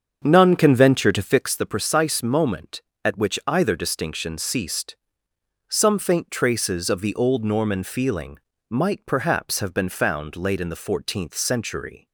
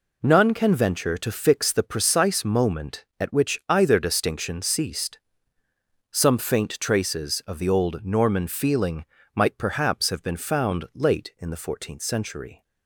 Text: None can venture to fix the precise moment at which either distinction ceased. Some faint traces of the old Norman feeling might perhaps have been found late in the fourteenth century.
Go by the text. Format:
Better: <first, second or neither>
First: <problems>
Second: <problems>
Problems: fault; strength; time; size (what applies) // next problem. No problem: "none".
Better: second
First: starts louder than the rest; strong; until 1.5 s; 7 dB // pauses between "feeling" and "might"; slight; at 8.3 s; 0.30 s long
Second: pauses between "feeling" and "might"; slight; at 9.0 s; 0.28 s long